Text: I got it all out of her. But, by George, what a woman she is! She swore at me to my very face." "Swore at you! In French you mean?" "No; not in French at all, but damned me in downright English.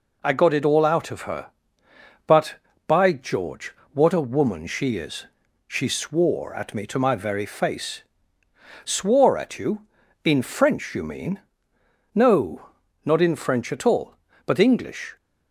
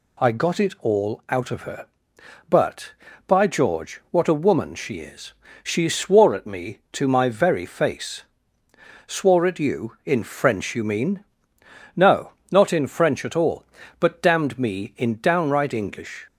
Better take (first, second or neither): second